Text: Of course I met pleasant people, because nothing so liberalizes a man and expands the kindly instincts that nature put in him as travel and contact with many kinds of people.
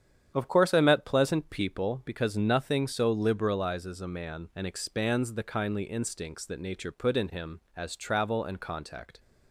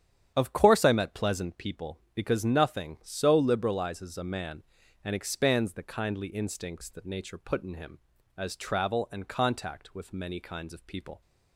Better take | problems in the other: second | starts louder than the rest; strong; until 1.3 s; 9 dB; strong in the second // stops before "with many kinds of people"; at 9.1 s

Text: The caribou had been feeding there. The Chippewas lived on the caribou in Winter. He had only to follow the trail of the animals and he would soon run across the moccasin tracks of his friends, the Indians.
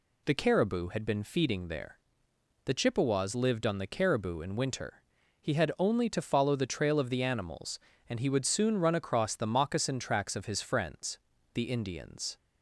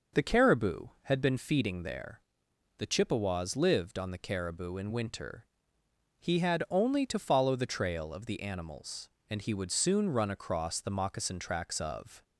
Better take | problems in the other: first | stops before "his friends the Indians"; at 12.2 s

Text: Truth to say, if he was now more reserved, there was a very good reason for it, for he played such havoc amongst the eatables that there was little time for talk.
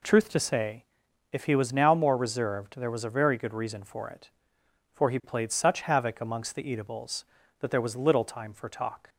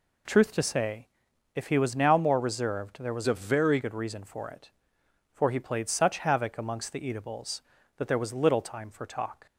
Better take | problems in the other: first | changes voice from "a" to "very"; from 3.2 to 3.7 s; 0.5 s long

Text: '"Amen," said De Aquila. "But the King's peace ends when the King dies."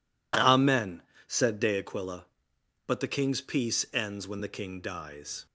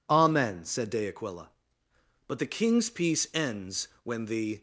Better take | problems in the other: first | stops before "King dies"; at 4.5 s

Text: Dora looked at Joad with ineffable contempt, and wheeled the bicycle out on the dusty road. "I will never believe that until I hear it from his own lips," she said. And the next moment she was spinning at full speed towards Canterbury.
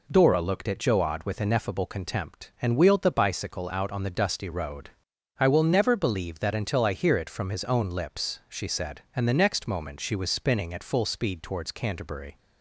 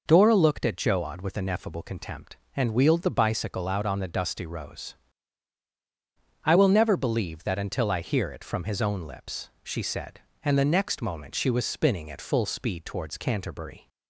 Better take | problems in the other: first | says "rose" for "road"; at 4.4 s

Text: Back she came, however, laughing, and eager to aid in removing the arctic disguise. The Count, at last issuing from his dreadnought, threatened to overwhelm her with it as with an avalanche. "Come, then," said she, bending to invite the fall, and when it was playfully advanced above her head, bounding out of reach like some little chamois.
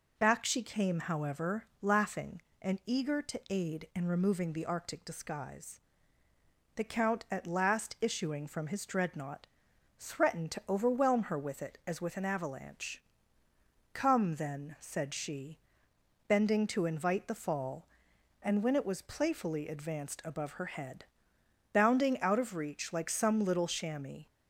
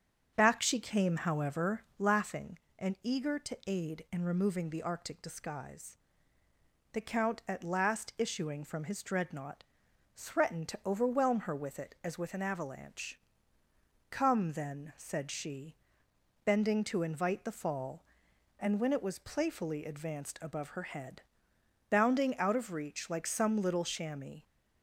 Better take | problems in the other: first | starts louder than the rest; until 2.2 s; 7 dB

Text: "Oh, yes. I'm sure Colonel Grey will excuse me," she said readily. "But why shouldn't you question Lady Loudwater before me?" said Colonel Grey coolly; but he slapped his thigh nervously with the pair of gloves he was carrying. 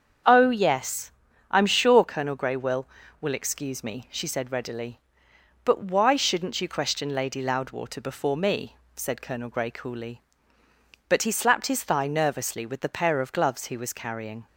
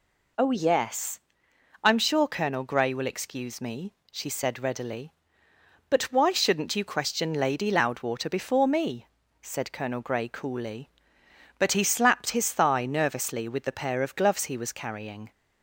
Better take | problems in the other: second | starts louder than the rest; strong; until 1.6 s; 7.5 dB // says "will" twice; at 3.2 s

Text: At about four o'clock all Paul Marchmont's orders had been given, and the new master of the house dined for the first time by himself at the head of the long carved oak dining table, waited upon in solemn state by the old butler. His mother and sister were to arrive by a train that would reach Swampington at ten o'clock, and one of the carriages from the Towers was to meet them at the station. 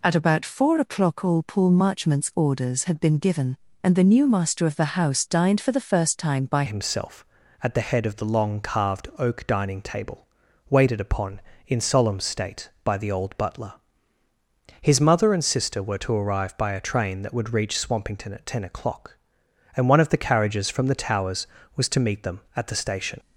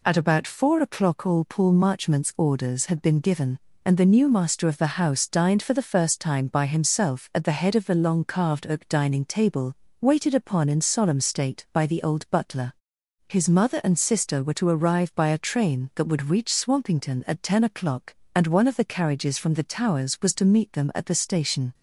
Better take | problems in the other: second | changes voice at "himself"; from 6.6 s on; 16.5 s long

